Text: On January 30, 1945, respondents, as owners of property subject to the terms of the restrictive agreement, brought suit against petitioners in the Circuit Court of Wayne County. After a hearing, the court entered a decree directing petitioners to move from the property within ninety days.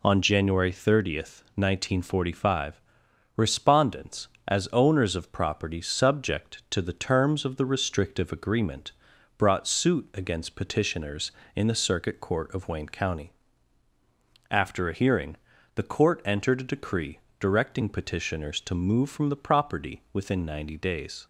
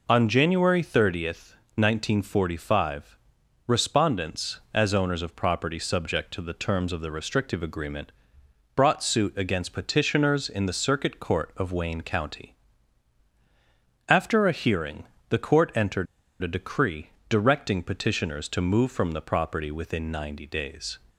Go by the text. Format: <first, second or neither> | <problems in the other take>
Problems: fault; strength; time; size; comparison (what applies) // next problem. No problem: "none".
first | pauses between "entered" and "a"; at 16.0 s; 0.36 s long // pauses between "decree" and "directing"; slight; at 17.1 s; 0.18 s long; slight in the first